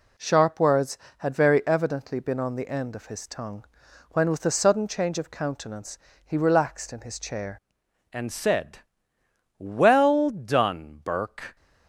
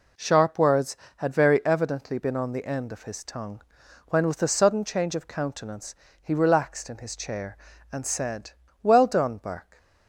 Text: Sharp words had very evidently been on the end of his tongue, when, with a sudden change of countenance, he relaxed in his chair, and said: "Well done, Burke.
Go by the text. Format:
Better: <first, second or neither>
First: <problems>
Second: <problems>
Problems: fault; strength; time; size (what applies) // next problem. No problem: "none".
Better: second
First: changes voice at "and"; from 8.1 s on; 3.4 s long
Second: none